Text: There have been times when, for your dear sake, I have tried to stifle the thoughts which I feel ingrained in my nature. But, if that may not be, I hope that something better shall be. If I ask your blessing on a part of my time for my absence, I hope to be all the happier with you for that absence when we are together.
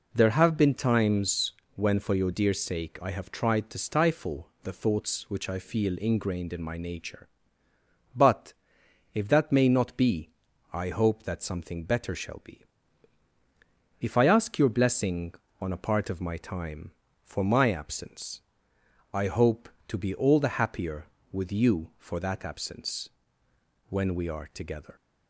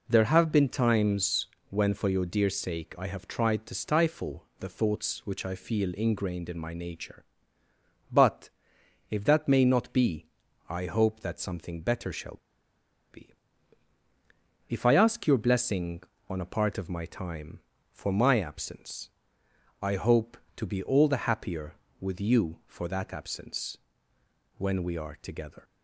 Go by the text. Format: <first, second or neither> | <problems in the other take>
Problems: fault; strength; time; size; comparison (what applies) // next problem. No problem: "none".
first | pauses between "times" and "when"; slight; at 1.4 s; 0.22 s long; slight in the first // pauses between "stifle" and "the"; slight; at 4.4 s; 0.16 s long; slight in the first // pauses between "shall" and "be"; noticeable; at 12.3 s; 0.75 s long // pauses between "absence" and "when"; noticeable; at 23.7 s; 0.80 s long; noticeable in the first